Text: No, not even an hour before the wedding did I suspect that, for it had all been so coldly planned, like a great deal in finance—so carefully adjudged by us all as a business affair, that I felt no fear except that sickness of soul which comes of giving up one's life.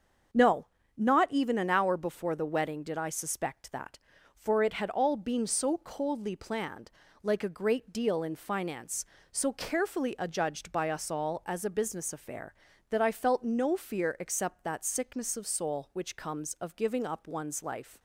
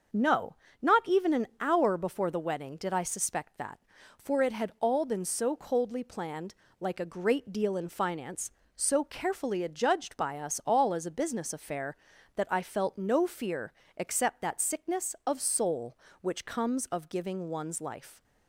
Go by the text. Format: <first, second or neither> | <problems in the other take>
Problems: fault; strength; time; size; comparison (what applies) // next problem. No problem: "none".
first | starts louder than the rest; until 1.4 s; 6.5 dB; also in the first // pauses between "fear" and "except"; slight; at 13.7 s; 0.24 s long // skips "up"; at 17.4 s